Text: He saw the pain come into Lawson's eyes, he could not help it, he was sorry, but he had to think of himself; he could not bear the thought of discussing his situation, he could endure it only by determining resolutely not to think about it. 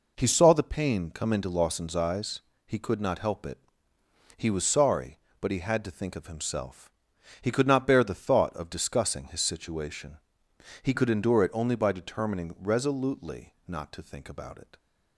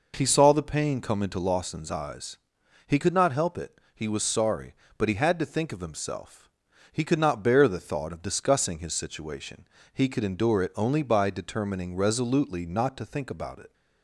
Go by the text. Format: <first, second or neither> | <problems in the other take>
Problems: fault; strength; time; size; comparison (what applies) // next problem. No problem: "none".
neither | none